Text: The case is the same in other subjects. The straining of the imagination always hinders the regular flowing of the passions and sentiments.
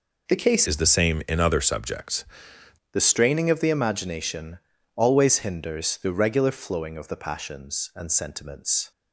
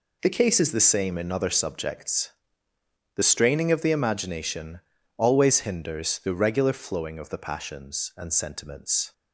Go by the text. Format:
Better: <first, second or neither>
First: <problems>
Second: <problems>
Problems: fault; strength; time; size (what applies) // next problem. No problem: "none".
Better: second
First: changes voice from "is" to "subjects"; from 0.6 to 2.2 s; 1.6 s long // pauses between "imagination" and "always"; at 4.5 s; 0.38 s long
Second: pauses between "imagination" and "always"; at 4.8 s; 0.38 s long